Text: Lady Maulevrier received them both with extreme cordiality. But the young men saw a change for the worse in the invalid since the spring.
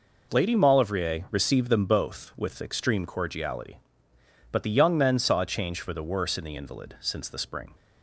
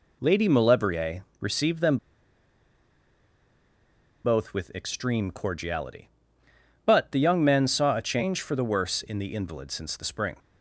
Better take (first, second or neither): first